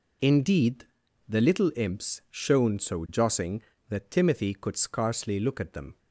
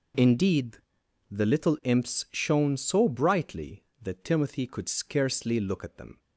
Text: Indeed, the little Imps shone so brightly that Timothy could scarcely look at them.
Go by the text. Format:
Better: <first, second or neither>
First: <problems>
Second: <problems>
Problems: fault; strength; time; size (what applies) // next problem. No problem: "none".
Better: second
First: says "jossing" for "brightly"; at 3.0 s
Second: none